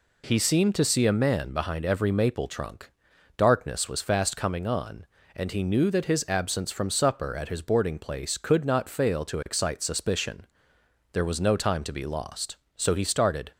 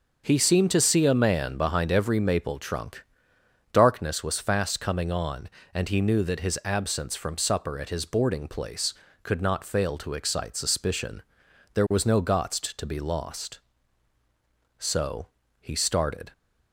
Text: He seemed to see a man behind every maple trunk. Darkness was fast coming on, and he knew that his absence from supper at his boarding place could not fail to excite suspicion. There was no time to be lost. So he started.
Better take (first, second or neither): first